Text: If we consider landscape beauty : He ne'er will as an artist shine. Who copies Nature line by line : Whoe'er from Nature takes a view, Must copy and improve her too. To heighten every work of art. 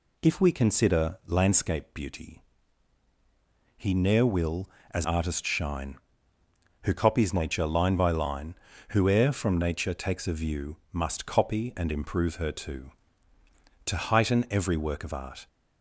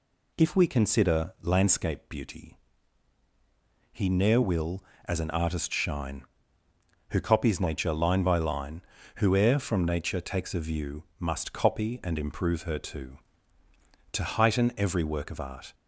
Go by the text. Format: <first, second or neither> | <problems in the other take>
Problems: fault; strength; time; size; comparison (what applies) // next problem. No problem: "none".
second | skips "an"; at 5.0 s